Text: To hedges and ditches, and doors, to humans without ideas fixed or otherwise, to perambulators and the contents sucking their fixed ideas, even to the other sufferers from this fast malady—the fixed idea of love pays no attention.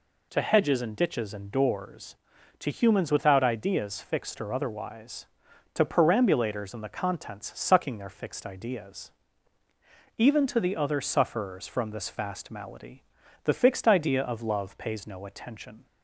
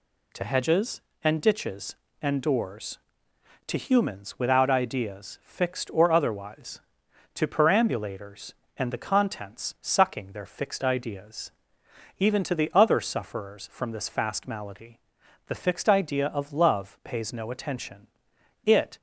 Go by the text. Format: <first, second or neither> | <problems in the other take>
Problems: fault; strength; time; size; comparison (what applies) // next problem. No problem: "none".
first | goes on to say "It"; slight; from 18.6 s on; 0.34 s long